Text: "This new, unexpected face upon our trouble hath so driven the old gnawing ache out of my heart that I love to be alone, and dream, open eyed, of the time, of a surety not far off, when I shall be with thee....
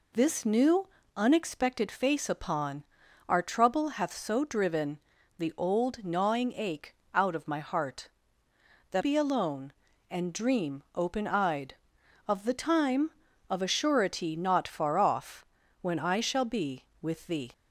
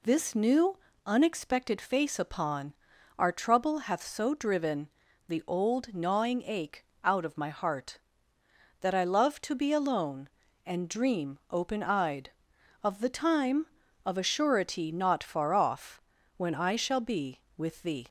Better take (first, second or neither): second